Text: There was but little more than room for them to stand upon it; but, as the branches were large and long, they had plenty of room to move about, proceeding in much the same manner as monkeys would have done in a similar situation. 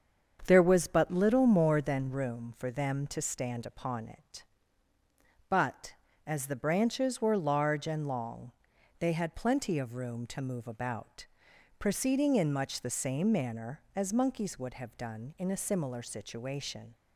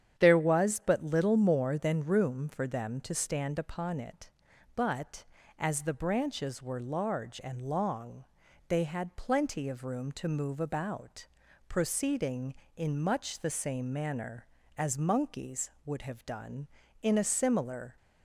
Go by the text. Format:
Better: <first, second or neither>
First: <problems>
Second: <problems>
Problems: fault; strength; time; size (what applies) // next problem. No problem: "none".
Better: first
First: starts louder than the rest; strong; until 1.4 s; 7.5 dB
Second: starts louder than the rest; strong; until 1.2 s; 9 dB // stops before "situation"; at 17.9 s